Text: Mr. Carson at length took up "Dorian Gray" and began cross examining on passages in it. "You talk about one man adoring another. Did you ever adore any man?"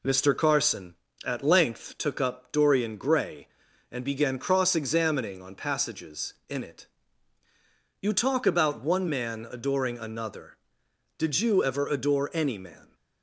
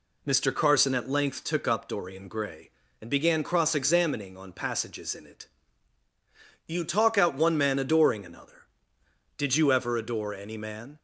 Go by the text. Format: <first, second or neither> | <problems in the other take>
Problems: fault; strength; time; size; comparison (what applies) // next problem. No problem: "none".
first | says "out" for "about"; at 7.1 s